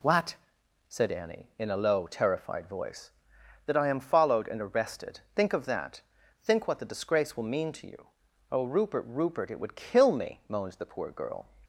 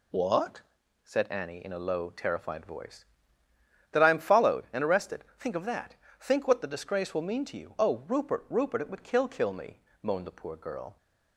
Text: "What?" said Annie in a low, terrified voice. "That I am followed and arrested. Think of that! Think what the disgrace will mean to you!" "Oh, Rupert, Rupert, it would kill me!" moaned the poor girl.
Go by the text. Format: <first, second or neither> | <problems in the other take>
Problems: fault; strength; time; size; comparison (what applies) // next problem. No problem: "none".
first | says "kill" twice; at 9.2 s